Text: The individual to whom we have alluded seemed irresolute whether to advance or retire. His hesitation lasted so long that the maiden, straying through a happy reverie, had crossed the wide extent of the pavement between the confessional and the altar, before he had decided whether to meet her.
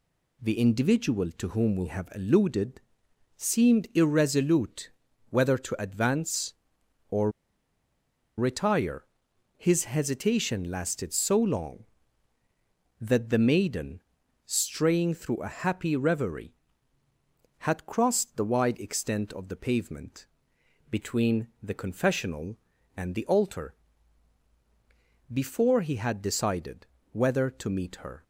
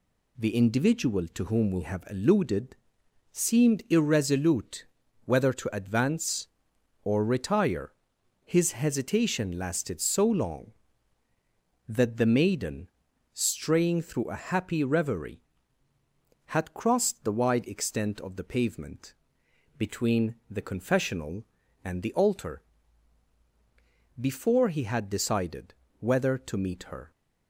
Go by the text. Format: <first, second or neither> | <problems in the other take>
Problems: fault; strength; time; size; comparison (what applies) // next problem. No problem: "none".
second | pauses between "alluded" and "seemed"; noticeable; at 2.8 s; 0.56 s long; noticeable in the second // pauses between "irresolute" and "whether"; at 4.9 s; 0.40 s long; also in the second // pauses between "or" and "retire"; at 7.3 s; 1.0 s long // pauses between "pavement" and "between"; noticeable; at 20.2 s; 0.64 s long; noticeable in the second // pauses between "decided" and "whether"; slight; at 26.8 s; 0.26 s long; slight in the second